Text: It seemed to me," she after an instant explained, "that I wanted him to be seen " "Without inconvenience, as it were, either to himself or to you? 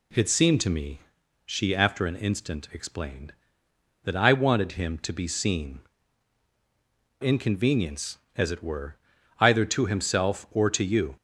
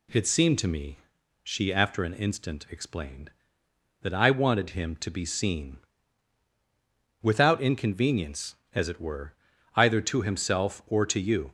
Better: second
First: skips "Without"; at 7.2 s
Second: none

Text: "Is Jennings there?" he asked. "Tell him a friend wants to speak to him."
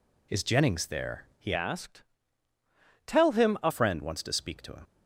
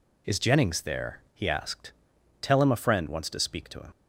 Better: second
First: changes voice from "asked" to "a"; from 1.5 to 3.7 s; 2.2 s long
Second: none

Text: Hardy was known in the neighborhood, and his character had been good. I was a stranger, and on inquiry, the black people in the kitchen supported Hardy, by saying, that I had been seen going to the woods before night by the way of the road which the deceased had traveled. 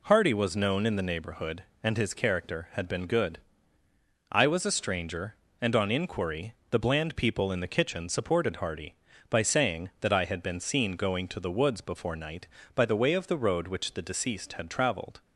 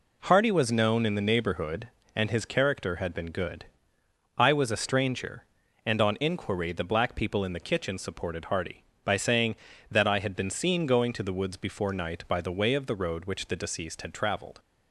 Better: second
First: says "bland" for "black"; at 6.7 s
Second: none

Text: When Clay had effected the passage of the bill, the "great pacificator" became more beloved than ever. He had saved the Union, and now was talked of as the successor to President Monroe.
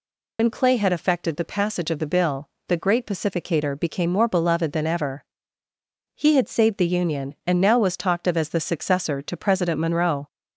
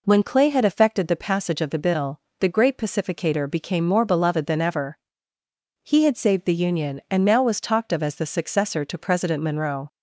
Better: second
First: loses the start of "When"; at 0.3 s; 105 ms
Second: none

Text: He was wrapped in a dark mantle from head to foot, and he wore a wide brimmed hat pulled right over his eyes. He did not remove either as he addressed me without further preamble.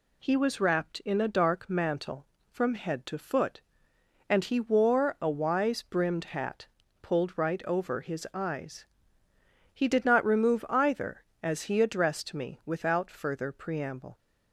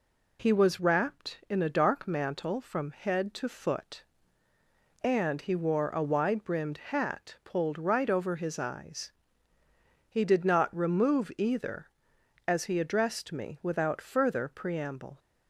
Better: second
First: says "wise" for "wide"; at 5.2 s // pauses between "hat" and "pulled"; slight; at 6.6 s; 0.36 s long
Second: none

